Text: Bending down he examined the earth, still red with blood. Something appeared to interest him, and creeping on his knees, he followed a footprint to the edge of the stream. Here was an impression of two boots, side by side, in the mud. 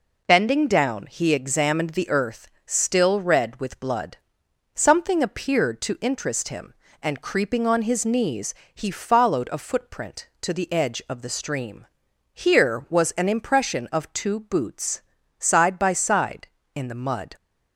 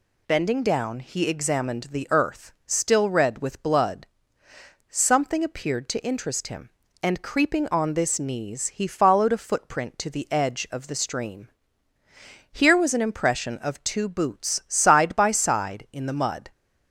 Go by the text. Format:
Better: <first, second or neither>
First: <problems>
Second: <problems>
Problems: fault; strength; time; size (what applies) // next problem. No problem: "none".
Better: first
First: none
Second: says "this" for "his"; at 7.9 s